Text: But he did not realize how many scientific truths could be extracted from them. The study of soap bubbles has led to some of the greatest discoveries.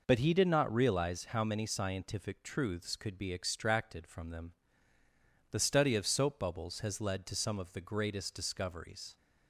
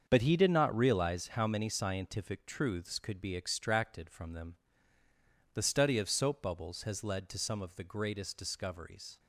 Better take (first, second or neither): first